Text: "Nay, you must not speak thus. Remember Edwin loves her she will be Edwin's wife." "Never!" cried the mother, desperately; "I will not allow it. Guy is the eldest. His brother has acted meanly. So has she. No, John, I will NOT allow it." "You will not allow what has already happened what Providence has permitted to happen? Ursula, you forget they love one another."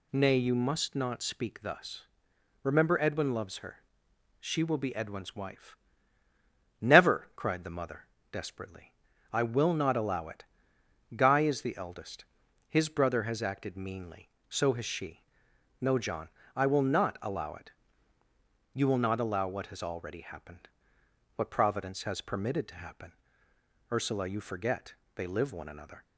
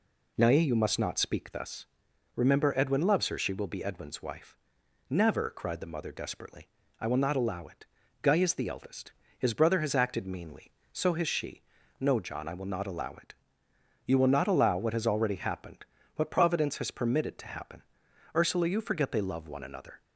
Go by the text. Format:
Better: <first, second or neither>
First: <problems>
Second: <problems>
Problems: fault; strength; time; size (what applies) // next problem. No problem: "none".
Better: second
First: pauses between "her" and "she"; noticeable; at 3.8 s; 0.60 s long // pauses between "happened" and "what"; noticeable; at 20.6 s; 0.66 s long // pauses between "forget" and "they"; slight; at 24.9 s; 0.20 s long // says "live" for "love"; at 25.2 s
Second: pauses between "happened" and "what"; slight; at 15.8 s; 0.30 s long